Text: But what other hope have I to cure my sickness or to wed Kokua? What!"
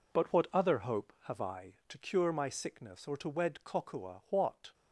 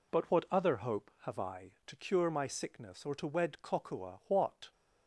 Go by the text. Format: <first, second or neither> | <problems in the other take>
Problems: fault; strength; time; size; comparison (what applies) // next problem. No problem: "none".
second | gets quieter; strong; throughout; 10 dB